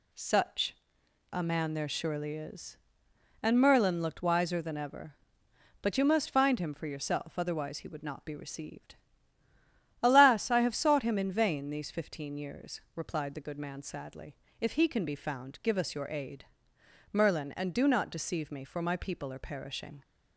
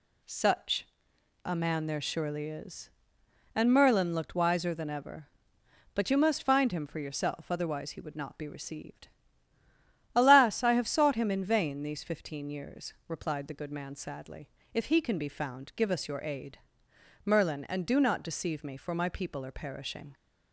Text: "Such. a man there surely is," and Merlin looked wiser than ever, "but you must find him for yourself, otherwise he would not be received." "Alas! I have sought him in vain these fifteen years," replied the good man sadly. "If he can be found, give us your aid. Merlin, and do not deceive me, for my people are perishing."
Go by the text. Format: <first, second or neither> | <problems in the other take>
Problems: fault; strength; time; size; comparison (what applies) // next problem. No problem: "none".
neither | none